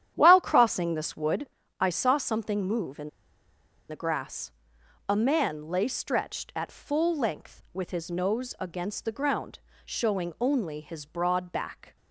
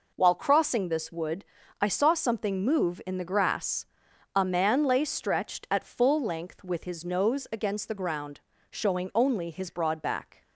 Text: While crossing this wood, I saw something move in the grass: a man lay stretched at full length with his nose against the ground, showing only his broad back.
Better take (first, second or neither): second